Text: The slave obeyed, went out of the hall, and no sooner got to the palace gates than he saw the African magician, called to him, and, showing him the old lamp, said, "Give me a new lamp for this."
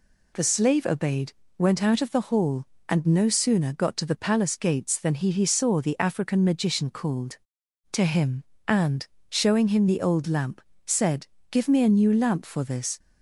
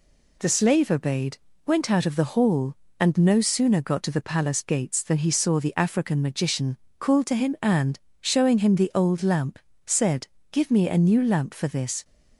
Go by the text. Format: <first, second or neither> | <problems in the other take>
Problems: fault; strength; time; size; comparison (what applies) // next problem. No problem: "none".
second | says "he" twice; at 5.3 s